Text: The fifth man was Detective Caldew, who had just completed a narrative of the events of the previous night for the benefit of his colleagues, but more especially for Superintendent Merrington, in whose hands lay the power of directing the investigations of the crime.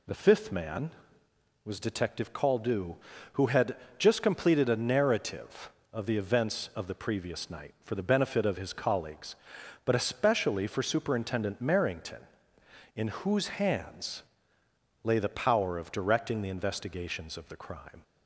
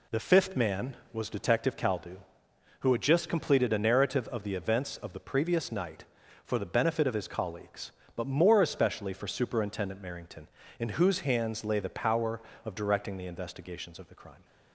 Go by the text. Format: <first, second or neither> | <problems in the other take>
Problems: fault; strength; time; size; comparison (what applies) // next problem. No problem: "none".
second | pauses between "had" and "just"; slight; at 3.7 s; 0.22 s long // skips "more"; at 9.9 s // pauses between "hands" and "lay"; noticeable; at 14.2 s; 0.82 s long